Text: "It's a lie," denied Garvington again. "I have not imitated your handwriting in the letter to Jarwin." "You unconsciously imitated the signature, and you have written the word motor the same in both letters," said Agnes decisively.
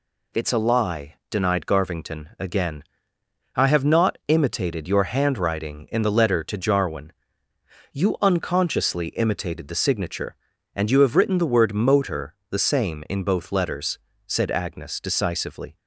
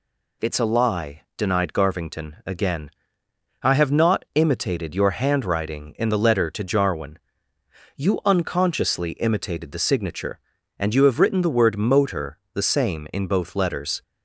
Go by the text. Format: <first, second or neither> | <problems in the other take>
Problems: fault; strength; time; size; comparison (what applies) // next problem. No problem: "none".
first | pauses between "motor" and "the"; slight; at 12.3 s; 0.16 s long; slight in the first // stops before "said Agnes decisively"; at 14.0 s